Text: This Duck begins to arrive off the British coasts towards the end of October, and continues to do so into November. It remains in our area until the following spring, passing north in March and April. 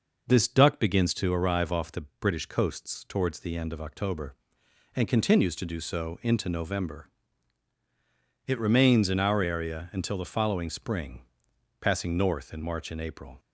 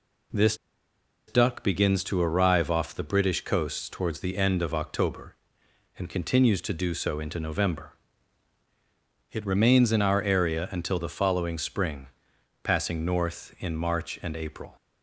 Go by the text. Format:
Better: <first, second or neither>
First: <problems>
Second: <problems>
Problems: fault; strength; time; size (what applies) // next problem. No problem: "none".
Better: first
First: none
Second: pauses between "This" and "Duck"; noticeable; at 0.5 s; 0.72 s long